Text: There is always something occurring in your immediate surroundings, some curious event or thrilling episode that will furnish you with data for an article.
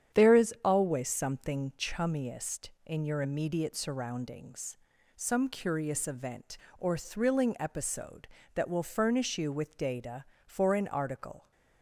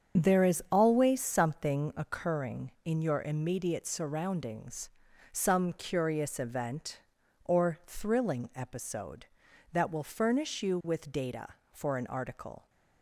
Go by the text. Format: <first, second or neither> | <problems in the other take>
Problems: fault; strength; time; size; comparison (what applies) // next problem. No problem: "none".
second | starts louder than the rest; strong; until 1.2 s; 9 dB; strong in the second // says "chummiest" for "occurring"; at 1.7 s